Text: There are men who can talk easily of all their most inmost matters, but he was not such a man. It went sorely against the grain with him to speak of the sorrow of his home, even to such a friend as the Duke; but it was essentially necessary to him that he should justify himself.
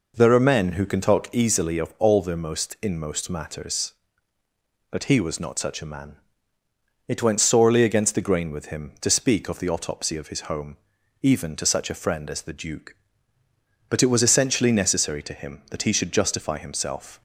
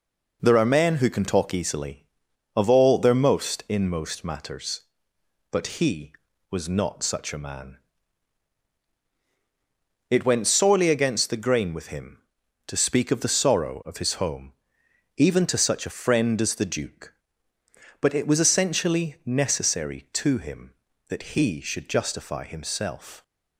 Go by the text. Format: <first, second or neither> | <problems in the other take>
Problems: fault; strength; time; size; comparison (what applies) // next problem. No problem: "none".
second | says "autopsy" for "sorrow"; at 9.6 s